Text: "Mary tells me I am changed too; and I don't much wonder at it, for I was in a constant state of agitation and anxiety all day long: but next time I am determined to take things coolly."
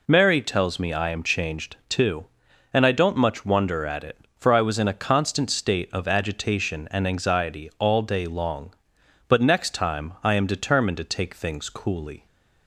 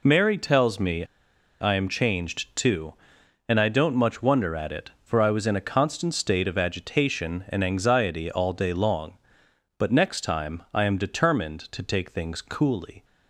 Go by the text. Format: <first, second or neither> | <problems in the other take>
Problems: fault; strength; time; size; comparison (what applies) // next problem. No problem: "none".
first | pauses between "me" and "I"; noticeable; at 1.0 s; 0.55 s long